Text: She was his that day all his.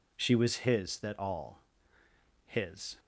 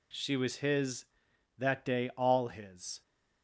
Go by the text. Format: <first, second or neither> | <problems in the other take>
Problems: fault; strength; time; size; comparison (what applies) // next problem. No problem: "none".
second | skips "day"; at 1.1 s // pauses between "all" and "his"; noticeable; at 1.6 s; 0.84 s long